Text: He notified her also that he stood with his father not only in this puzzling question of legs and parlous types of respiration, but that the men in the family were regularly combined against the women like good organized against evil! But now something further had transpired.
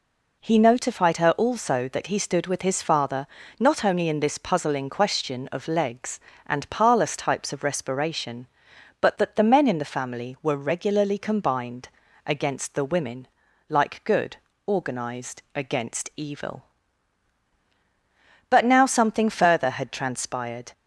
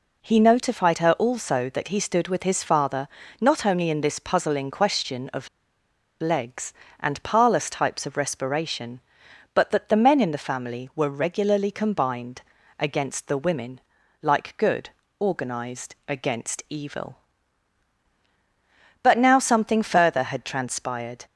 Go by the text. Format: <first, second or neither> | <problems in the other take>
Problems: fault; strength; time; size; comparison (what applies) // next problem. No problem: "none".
first | pauses between "father" and "not"; slight; at 3.0 s; 0.34 s long; slight in the first // pauses between "of" and "legs"; noticeable; at 5.4 s; 0.73 s long // pauses between "combined" and "against"; slight; at 12.4 s; 0.36 s long; slight in the first // pauses between "women" and "like"; at 13.7 s; 0.42 s long; also in the first // pauses between "good" and "organized"; slight; at 14.8 s; 0.30 s long; slight in the first